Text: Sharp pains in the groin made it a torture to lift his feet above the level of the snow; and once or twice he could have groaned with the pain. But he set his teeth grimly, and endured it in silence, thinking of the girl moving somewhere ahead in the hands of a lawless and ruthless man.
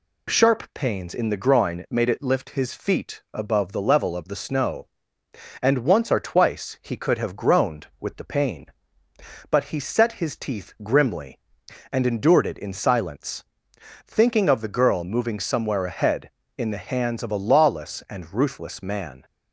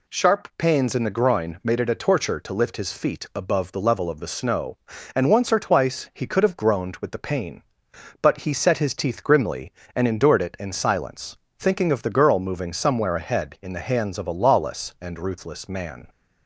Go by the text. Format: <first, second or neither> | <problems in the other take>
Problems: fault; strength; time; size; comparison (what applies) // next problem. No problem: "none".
second | skips "a torture to"; at 2.2 s